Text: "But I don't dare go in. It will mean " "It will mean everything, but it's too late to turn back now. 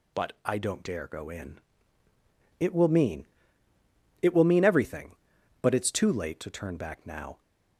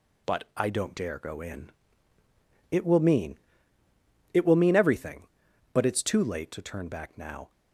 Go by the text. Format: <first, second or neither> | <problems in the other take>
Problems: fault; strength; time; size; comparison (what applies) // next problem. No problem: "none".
first | gets quieter; noticeable; throughout; 4 dB